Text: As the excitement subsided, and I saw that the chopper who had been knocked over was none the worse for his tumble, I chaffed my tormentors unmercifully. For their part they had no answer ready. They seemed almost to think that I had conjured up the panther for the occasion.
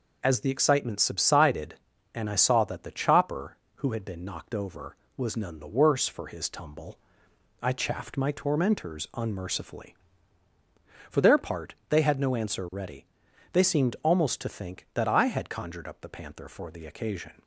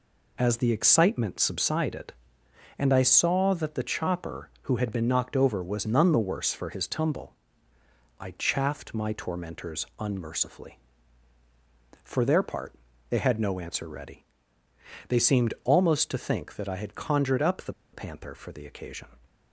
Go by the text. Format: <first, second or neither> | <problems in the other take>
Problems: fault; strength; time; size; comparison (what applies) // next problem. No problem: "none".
first | pauses between "part" and "they"; slight; at 12.7 s; 0.34 s long; slight in the first // pauses between "the" and "panther"; slight; at 17.7 s; 0.20 s long